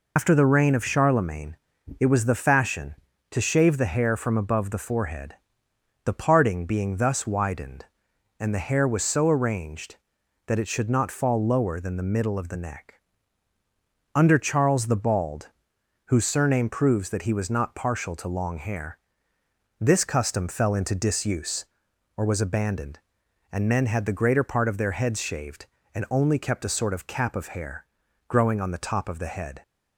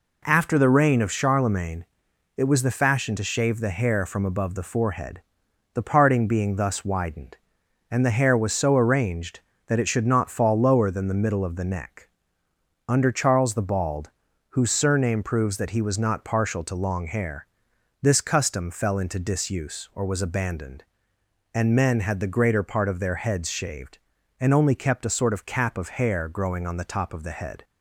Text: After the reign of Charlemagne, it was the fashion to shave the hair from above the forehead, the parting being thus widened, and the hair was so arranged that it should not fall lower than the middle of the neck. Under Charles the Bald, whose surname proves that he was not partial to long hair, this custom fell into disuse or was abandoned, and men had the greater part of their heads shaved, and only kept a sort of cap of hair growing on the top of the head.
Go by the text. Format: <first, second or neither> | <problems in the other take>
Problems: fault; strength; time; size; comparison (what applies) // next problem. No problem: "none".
second | loses the start of "After"; at 0.1 s; 100 ms // pauses between "hair" and "growing"; at 27.8 s; 0.40 s long